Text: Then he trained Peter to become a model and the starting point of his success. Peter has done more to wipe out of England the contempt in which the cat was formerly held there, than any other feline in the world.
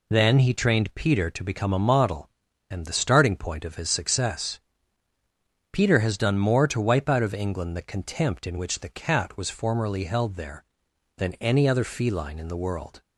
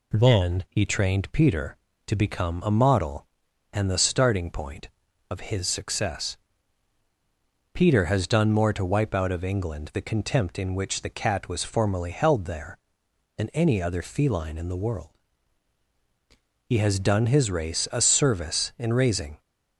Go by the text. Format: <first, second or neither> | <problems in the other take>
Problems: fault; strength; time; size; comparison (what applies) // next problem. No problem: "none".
first | goes on to say "He has done his race a service in raising"; strong; from 16.6 s on; 2.7 s long